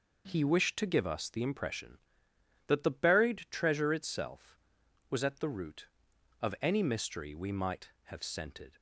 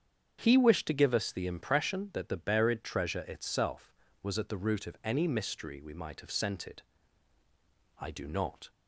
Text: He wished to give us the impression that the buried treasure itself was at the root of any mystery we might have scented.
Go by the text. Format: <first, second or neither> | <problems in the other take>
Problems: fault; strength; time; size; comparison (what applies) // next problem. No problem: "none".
first | starts louder than the rest; strong; until 1.4 s; 8 dB // goes on to say "I do not"; noticeable; from 7.9 s on; 0.70 s long